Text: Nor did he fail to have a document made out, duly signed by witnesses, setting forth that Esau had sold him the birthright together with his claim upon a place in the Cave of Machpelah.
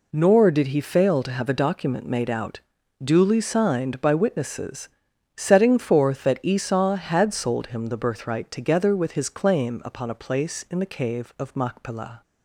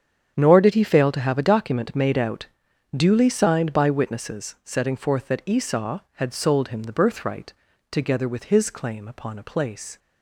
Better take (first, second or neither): first